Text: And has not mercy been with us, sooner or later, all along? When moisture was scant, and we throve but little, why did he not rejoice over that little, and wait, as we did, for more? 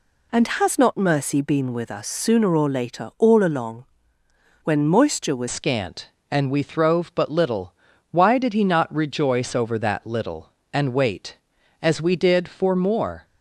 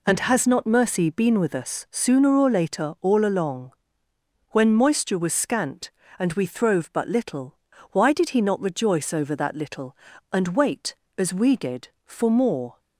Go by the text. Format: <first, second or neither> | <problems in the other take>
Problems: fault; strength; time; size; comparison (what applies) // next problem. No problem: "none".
second | changes voice at "scant"; from 5.4 s on; 7.8 s long